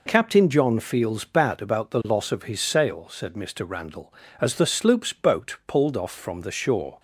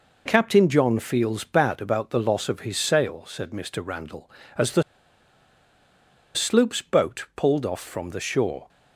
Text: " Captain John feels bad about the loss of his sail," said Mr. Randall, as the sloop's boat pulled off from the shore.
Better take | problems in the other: first | pauses between "the" and "sloop's"; strong; at 4.8 s; 1.5 s long

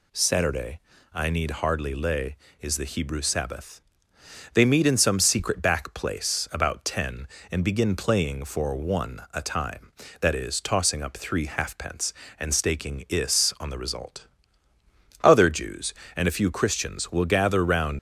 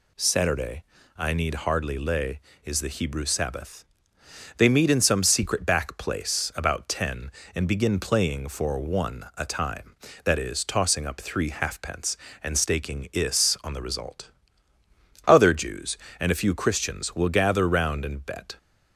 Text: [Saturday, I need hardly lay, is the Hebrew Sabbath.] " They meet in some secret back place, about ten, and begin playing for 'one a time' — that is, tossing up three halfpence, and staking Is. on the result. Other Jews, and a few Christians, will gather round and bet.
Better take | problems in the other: second | stops before "and bet"; at 17.9 s

